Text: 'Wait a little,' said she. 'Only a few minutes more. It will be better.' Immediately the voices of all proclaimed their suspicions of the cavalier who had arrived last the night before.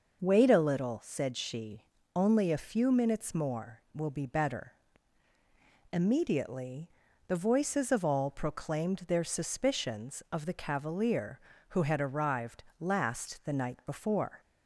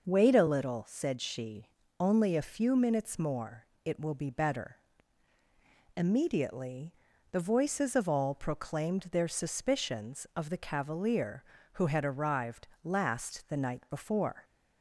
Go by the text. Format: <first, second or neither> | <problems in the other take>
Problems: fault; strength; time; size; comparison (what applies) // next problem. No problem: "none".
second | skips "It"; at 3.8 s // pauses between "Immediately" and "the"; at 6.8 s; 0.40 s long; also in the second // pauses between "arrived" and "last"; slight; at 12.6 s; 0.16 s long; slight in the second